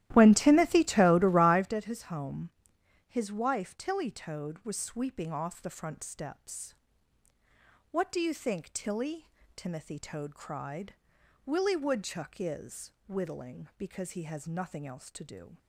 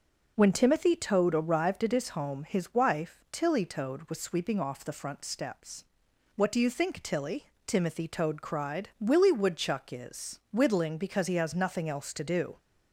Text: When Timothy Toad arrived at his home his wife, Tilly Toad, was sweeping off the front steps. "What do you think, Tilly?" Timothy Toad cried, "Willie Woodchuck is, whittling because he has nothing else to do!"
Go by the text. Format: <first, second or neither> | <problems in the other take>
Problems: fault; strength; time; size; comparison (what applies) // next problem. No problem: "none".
second | starts louder than the rest; strong; until 1.8 s; 13.5 dB // pauses between "home" and "his"; noticeable; at 2.4 s; 0.58 s long